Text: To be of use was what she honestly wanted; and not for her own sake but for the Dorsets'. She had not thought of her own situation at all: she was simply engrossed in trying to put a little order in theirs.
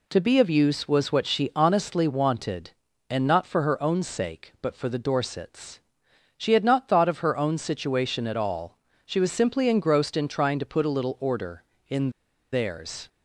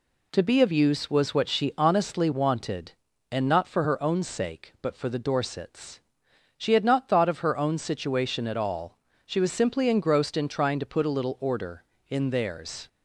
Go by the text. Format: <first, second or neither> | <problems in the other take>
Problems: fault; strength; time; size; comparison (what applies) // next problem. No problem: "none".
second | pauses between "in" and "theirs"; at 12.1 s; 0.41 s long